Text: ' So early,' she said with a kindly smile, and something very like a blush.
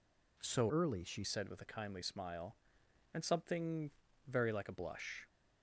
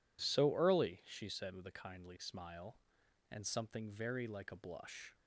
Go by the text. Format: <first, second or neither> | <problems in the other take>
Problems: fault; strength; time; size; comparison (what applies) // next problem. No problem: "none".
second | changes voice from "early" to "she"; from 0.6 to 1.2 s; 0.6 s long // pauses between "something" and "very"; at 3.9 s; 0.38 s long